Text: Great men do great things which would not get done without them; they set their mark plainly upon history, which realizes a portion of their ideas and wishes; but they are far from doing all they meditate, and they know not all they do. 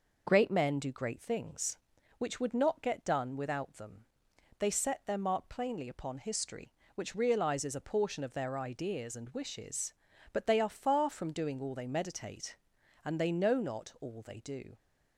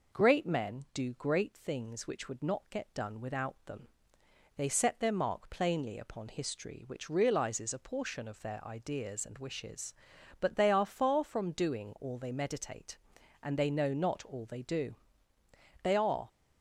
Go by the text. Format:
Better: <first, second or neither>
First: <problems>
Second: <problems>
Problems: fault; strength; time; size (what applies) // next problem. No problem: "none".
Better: first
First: none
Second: goes on to say "They are"; slight; from 15.8 s on; 0.46 s long